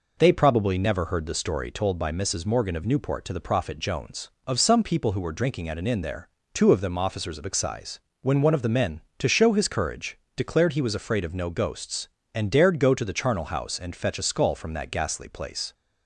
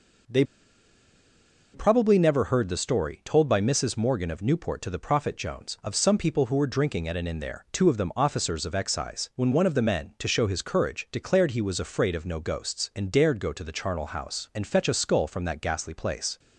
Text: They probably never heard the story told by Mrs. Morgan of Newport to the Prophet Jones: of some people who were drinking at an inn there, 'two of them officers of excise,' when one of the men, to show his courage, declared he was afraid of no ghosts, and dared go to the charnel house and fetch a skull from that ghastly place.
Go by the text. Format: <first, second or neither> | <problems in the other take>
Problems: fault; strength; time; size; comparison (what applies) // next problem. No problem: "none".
first | pauses between "They" and "probably"; strong; at 0.4 s; 1.3 s long